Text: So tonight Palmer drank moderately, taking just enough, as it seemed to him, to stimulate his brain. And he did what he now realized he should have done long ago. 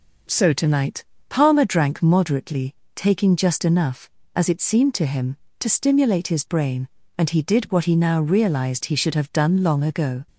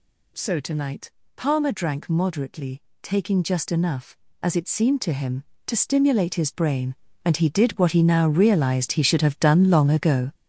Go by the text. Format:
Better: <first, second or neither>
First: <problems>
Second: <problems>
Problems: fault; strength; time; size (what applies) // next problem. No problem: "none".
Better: first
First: pauses between "tonight" and "Palmer"; slight; at 1.0 s; 0.24 s long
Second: gets louder; strong; throughout; 8 dB // pauses between "tonight" and "Palmer"; slight; at 1.1 s; 0.24 s long